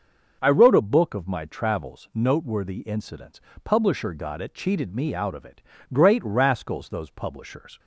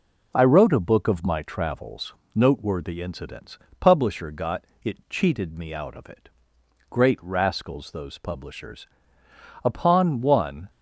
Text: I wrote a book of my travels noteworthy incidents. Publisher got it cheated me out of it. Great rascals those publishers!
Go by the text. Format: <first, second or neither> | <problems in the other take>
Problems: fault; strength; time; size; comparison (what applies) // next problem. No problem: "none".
first | pauses between "travels" and "noteworthy"; slight; at 2.1 s; 0.20 s long // pauses between "got" and "it"; slight; at 4.6 s; 0.18 s long // goes on to say "Upon one"; noticeable; from 9.6 s on; 1.0 s long